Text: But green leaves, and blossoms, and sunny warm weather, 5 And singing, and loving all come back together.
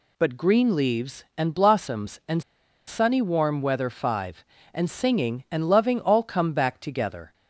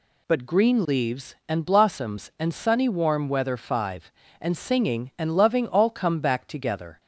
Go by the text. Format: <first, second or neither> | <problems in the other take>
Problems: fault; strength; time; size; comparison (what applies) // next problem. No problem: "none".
second | pauses between "and" and "sunny"; noticeable; at 2.4 s; 0.46 s long